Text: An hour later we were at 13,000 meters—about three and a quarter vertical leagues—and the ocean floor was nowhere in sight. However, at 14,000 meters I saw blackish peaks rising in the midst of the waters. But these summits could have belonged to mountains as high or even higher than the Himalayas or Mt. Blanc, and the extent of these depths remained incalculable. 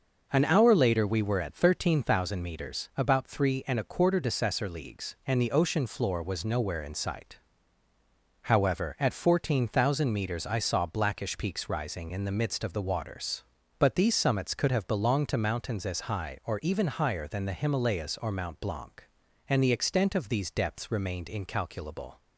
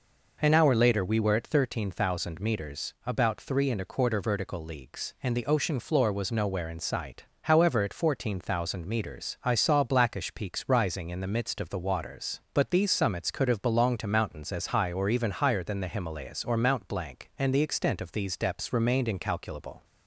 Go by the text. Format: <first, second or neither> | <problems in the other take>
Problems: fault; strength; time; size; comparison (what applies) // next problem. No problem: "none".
second | says "decessor" for "vertical"; at 4.1 s